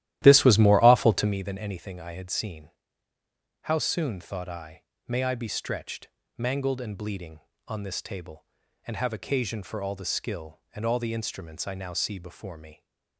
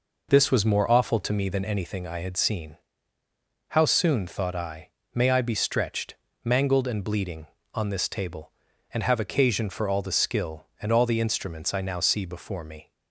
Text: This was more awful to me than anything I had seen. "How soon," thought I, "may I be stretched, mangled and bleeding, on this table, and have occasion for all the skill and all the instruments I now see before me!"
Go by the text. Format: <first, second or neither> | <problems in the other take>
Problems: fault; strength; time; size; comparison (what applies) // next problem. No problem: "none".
second | starts louder than the rest; strong; until 1.4 s; 13.5 dB